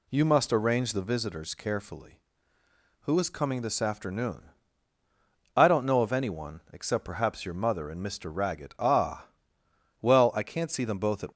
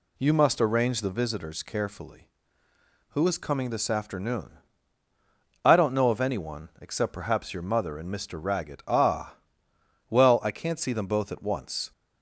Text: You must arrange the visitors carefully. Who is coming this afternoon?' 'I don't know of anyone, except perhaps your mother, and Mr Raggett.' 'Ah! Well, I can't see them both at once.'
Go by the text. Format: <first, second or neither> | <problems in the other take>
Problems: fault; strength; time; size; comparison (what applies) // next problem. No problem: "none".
second | stops before "once"; at 11.3 s